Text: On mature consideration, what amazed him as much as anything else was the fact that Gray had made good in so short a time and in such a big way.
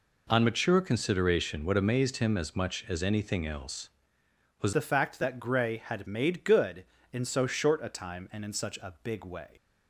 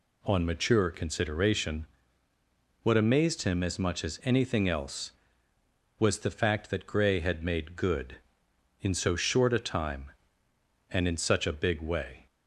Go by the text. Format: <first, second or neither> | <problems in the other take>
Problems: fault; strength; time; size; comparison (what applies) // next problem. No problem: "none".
second | changes voice at "the"; from 4.7 s on; 4.7 s long